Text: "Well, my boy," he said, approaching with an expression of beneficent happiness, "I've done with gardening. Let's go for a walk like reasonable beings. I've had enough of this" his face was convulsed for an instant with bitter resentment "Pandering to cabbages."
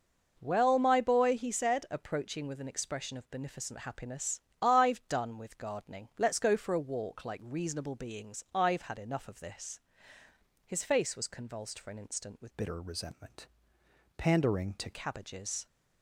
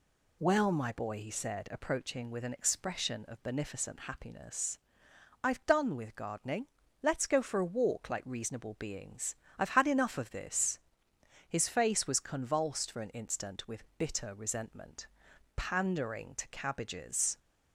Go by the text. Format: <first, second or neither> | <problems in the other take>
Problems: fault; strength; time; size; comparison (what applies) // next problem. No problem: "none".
second | pauses between "this" and "his"; noticeable; at 9.7 s; 0.84 s long; noticeable in the second // changes voice from "bitter" to "to"; from 12.5 to 14.9 s; 2.4 s long // pauses between "resentment" and "Pandering"; noticeable; at 13.4 s; 0.70 s long; noticeable in the second